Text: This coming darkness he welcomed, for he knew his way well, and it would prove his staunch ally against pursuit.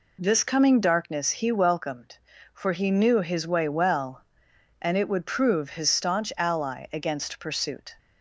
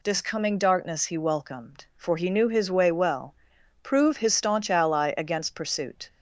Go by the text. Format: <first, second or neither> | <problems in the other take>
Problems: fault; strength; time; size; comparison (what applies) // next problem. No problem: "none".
first | skips "and it would"; at 3.5 s